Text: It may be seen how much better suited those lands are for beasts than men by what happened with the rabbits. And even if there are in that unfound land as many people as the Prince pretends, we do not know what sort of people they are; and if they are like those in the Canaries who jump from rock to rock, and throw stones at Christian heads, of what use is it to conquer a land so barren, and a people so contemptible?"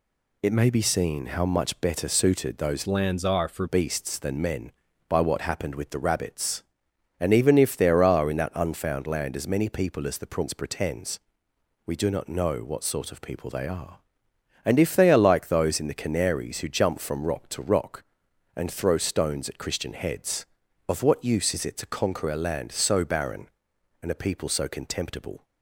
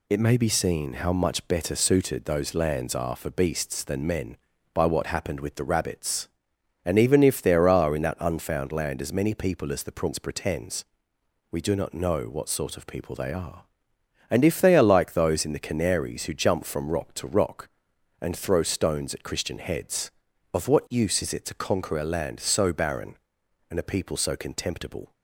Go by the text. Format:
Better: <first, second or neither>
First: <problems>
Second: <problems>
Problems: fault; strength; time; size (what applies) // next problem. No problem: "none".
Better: second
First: changes voice from "lands" to "for"; from 2.8 to 3.6 s; 0.8 s long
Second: none